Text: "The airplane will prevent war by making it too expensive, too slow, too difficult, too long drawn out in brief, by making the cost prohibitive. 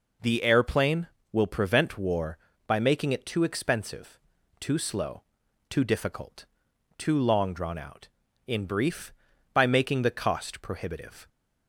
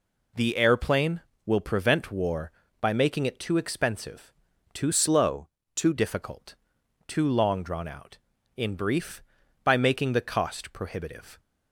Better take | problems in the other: first | changes voice from "slow" to "too"; from 4.9 to 5.9 s; 1.0 s long

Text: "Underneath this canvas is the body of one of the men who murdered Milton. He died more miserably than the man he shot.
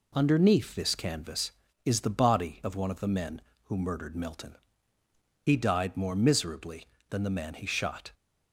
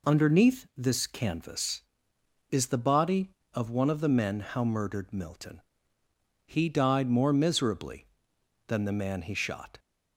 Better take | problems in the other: first | says "how" for "who"; at 4.4 s

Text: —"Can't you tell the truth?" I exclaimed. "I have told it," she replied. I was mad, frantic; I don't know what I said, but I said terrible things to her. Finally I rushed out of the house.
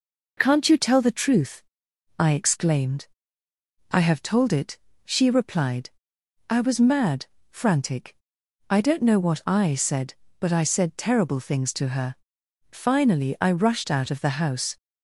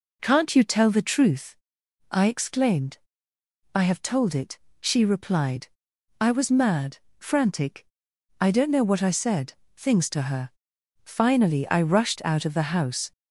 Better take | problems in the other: first | skips "but I said terrible"; at 9.6 s

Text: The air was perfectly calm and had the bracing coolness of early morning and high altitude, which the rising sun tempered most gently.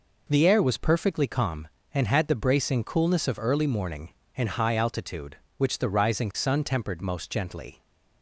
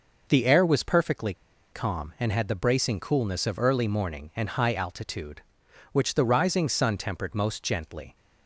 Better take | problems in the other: first | pauses between "perfectly" and "calm"; at 1.3 s; 0.40 s long

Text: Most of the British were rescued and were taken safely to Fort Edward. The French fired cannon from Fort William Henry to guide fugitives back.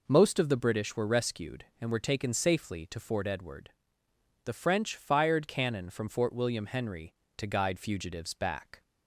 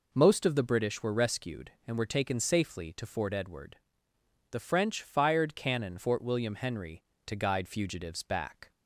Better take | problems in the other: first | skips "from"; at 5.9 s

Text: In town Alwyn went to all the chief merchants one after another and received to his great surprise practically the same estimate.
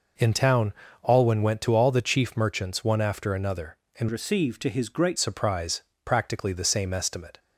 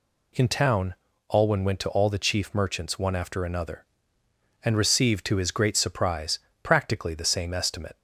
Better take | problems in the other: second | pauses between "town" and "Alwyn"; slight; at 0.7 s; 0.34 s long; slight in the second // changes voice from "received" to "great"; from 4.0 to 5.1 s; 1.1 s long // pauses between "surprise" and "practically"; slight; at 5.8 s; 0.22 s long; slight in the second

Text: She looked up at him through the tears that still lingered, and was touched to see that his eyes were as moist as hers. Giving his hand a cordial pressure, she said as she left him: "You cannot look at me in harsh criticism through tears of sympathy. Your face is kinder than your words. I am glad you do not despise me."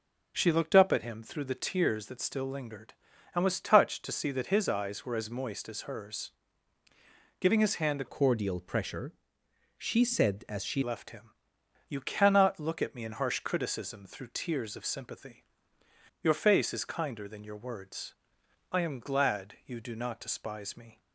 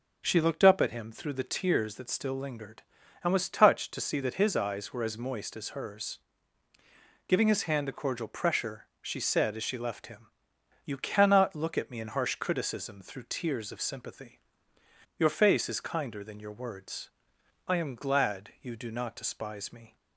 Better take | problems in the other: second | starts louder than the rest; noticeable; until 1.3 s; 6 dB // changes voice from "cordial" to "she"; from 8.0 to 10.8 s; 2.8 s long

